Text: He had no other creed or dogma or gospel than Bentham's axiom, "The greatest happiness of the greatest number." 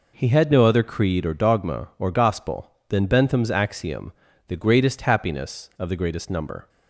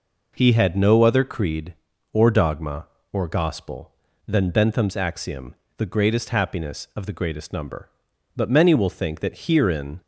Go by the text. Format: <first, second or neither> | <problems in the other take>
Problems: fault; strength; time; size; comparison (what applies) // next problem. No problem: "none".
first | goes on to say "But many will think that herein"; from 8.3 s on; 1.6 s long